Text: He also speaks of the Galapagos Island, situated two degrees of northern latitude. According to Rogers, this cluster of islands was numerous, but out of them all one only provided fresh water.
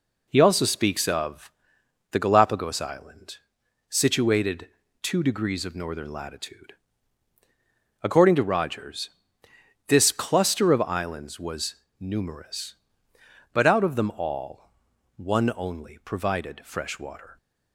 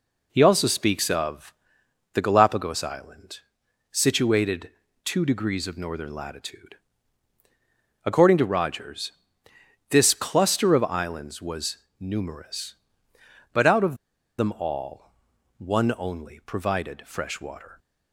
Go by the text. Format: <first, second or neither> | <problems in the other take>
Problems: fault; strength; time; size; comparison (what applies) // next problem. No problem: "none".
first | pauses between "of" and "the"; noticeable; at 1.5 s; 0.60 s long; noticeable in the first // pauses between "situated" and "two"; slight; at 4.6 s; 0.34 s long; slight in the first // pauses between "was" and "numerous"; slight; at 11.7 s; 0.20 s long; slight in the first // pauses between "of" and "them"; at 13.9 s; 0.41 s long // pauses between "all" and "one"; noticeable; at 15.1 s; 0.48 s long; noticeable in the first